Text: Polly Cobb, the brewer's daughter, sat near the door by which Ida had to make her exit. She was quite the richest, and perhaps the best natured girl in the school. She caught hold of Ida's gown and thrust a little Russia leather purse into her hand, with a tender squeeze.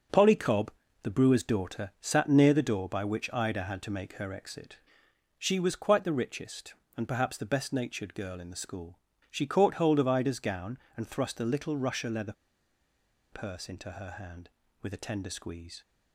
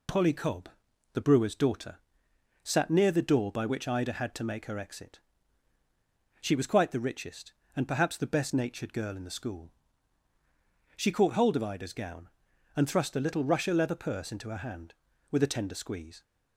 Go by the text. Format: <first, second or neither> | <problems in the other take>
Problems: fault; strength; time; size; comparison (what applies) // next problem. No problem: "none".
second | starts louder than the rest; until 1.4 s; 6 dB // pauses between "leather" and "purse"; noticeable; at 12.3 s; 0.97 s long